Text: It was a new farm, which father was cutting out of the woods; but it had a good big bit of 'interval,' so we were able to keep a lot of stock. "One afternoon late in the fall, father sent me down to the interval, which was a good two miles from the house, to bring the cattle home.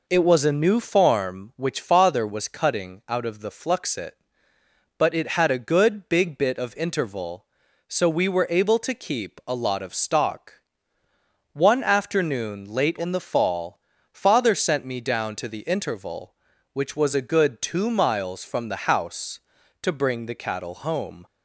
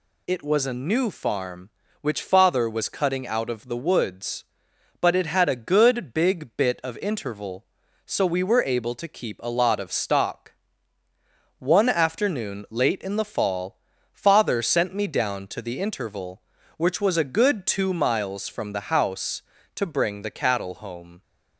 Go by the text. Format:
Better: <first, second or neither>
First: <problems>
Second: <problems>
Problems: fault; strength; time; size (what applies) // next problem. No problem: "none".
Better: second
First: says "fluxit" for "woods"; at 3.4 s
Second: none